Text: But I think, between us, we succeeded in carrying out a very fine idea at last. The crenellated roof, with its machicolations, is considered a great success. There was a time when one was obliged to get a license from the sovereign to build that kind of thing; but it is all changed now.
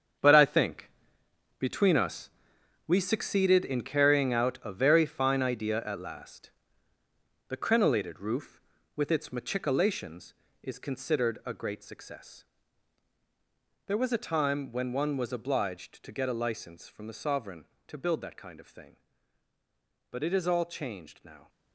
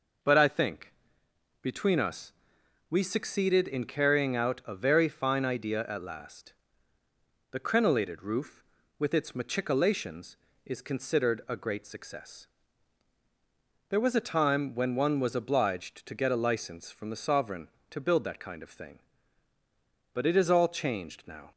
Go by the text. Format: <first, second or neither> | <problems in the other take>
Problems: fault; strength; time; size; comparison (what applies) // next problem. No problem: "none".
second | gets quieter; strong; throughout; 11 dB